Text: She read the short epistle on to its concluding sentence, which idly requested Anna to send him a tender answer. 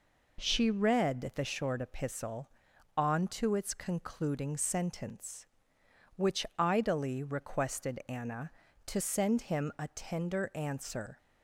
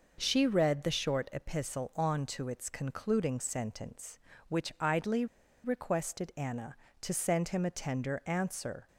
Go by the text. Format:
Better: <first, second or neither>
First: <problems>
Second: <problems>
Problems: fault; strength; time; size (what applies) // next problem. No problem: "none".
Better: first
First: none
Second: pauses between "idly" and "requested"; at 5.2 s; 0.39 s long